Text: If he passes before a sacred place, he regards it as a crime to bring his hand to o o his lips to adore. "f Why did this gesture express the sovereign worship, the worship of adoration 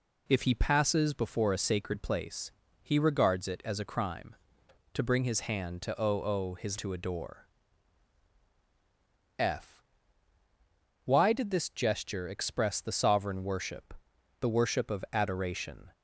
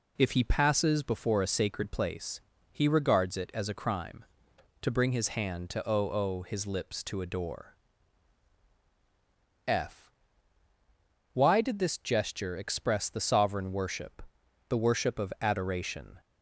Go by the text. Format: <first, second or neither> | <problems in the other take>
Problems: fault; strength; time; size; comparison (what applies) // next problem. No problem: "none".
second | skips "lips"; at 6.7 s // pauses between "f" and "Why"; at 9.8 s; 1.2 s long; also in the second